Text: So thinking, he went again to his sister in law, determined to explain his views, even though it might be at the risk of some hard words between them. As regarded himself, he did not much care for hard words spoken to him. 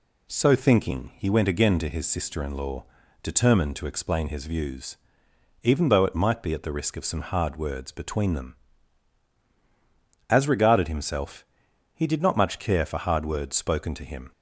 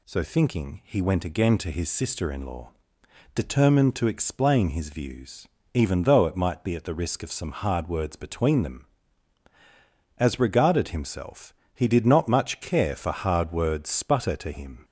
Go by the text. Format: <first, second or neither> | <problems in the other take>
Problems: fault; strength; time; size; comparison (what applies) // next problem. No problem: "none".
first | says "sputter" for "spoken"; at 13.8 s